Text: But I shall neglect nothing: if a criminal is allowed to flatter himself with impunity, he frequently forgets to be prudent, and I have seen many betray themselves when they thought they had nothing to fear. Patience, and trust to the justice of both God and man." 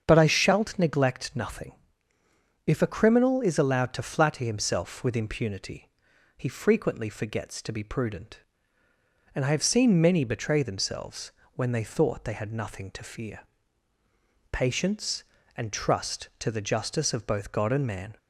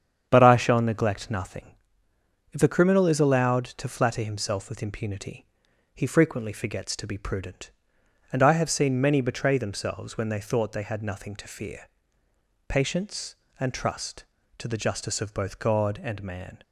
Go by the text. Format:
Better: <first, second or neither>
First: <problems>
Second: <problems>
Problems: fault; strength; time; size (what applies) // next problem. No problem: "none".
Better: second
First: starts louder than the rest; strong; until 1.0 s; 7.5 dB // says "shalt" for "shall"; at 0.2 s // pauses between "themselves" and "when"; slight; at 11.3 s; 0.22 s long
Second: starts louder than the rest; strong; until 1.3 s; 8.5 dB